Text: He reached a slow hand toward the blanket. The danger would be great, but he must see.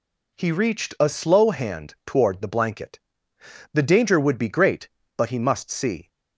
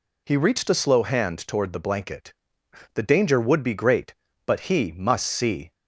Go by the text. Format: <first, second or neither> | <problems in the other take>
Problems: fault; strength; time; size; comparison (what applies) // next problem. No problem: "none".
neither | none